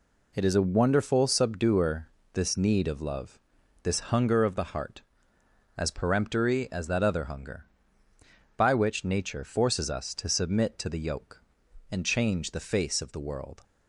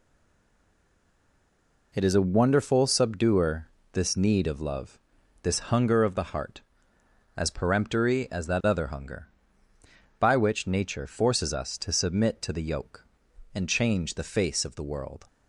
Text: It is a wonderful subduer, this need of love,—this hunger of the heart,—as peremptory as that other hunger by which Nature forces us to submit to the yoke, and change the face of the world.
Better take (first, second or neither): first